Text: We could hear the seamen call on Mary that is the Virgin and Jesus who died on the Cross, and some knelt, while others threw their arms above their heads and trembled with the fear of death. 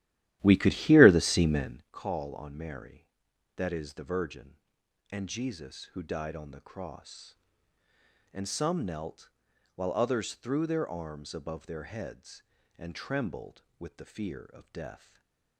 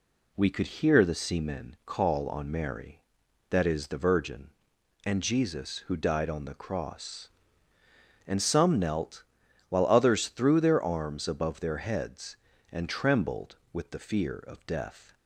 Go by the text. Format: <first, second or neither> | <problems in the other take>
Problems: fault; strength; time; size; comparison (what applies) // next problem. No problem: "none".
second | starts louder than the rest; strong; until 1.9 s; 13 dB // stays silent after the last word; slight; from 14.9 s on; 0.6 s long